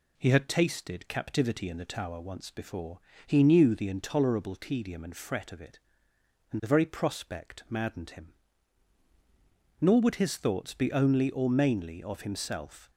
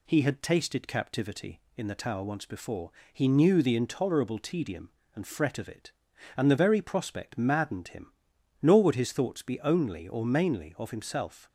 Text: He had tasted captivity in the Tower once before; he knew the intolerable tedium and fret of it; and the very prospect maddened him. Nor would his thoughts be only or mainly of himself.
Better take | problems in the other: neither | none

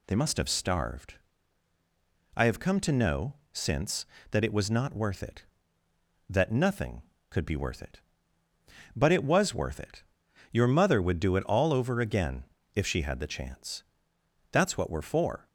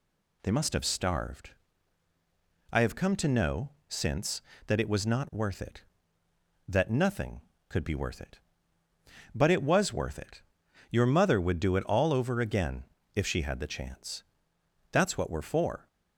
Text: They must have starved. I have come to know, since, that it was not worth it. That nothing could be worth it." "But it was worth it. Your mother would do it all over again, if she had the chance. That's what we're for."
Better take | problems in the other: neither | none

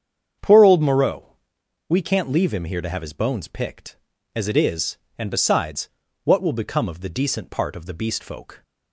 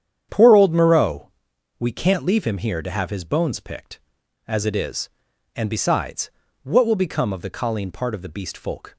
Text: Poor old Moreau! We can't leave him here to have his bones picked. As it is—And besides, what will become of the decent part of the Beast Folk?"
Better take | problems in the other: first | starts louder than the rest; strong; until 1.3 s; 9 dB; strong in the first // says "colleen" for "decent"; at 7.4 s

